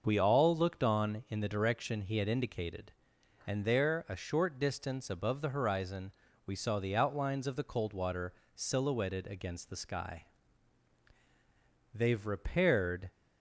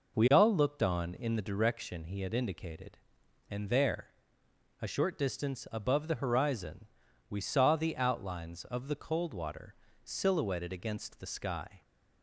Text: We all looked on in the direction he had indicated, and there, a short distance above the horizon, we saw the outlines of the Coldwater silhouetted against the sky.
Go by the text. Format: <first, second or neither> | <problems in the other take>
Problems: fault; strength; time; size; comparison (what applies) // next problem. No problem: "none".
second | starts louder than the rest; noticeable; until 1.0 s; 6 dB // pauses between "Coldwater" and "silhouetted"; slight; at 8.3 s; 0.20 s long; slight in the second // goes on to say "They've repaired"; noticeable; from 11.9 s on; 1.1 s long